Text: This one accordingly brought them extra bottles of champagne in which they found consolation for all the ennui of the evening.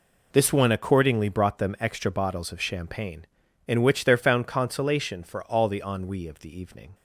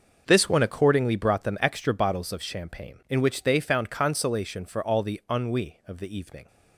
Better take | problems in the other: second | says "there" for "they"; at 4.0 s

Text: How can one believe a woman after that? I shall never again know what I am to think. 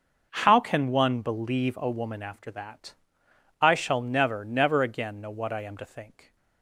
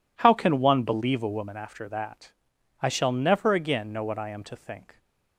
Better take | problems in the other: second | starts louder than the rest; until 1.3 s; 6.5 dB // says "never" twice; at 4.4 s

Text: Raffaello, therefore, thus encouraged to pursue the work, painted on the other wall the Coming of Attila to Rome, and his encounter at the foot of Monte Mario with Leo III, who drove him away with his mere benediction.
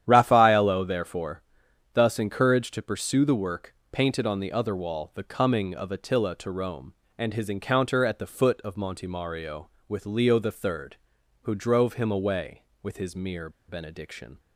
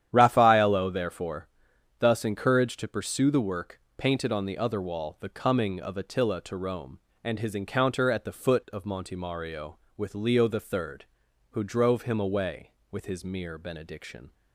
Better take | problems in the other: second | starts louder than the rest; strong; until 1.0 s; 10 dB; strong in the second // pauses between "mere" and "benediction"; slight; at 13.4 s; 0.19 s long

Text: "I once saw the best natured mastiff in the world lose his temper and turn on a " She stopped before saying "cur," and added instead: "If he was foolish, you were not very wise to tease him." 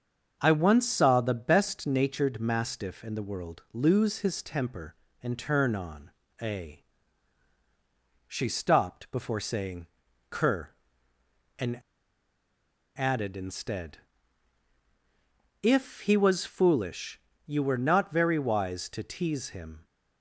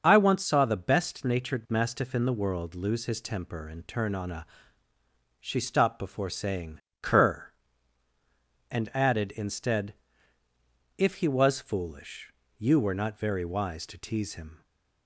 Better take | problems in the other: second | starts louder than the rest; strong; until 1.4 s; 7.5 dB; also in the second // pauses between "on" and "a"; slight; at 6.1 s; 0.28 s long // pauses between "saying" and "cur"; at 9.8 s; 0.42 s long; slight in the second // pauses between "and" and "added"; at 11.8 s; 1.1 s long

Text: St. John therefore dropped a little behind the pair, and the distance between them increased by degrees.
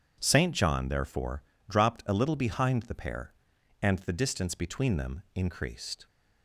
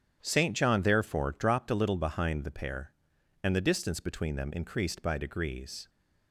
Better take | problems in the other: second | starts louder than the rest; strong; until 1.2 s; 8.5 dB; strong in the second // pauses between "therefore" and "dropped"; slight; at 1.4 s; 0.26 s long // stops before "by degrees"; at 6.0 s

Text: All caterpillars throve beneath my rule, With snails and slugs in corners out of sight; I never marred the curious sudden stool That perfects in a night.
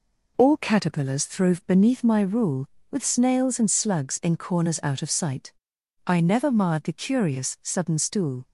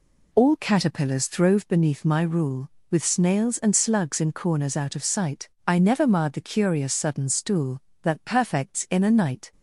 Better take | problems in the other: second | stops before "That perfects in a night"; at 8.4 s

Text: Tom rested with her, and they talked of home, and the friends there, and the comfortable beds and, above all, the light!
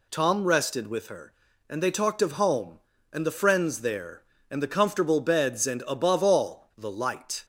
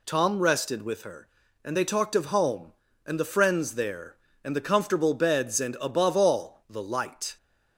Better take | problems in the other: neither | none

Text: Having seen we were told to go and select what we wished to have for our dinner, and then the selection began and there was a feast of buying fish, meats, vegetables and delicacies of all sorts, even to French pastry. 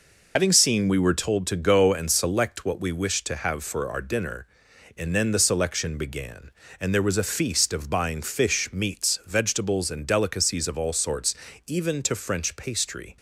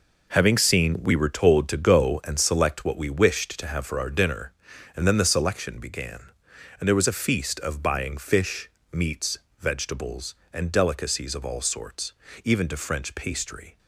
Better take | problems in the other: second | loses the start of "Having"; at 0.3 s; 65 ms

